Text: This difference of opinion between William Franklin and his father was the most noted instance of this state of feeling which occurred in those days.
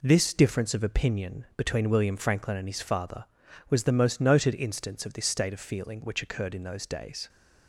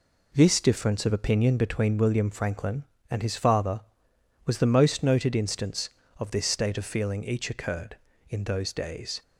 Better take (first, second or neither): first